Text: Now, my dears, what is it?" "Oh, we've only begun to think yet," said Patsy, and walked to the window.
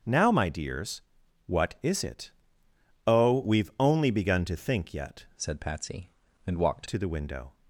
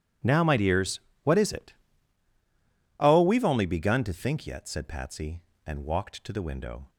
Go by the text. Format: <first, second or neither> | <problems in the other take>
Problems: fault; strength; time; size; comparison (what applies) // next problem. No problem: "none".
second | starts louder than the rest; strong; until 1.5 s; 7.5 dB // changes voice from "said" to "walked"; from 5.3 to 6.8 s; 1.5 s long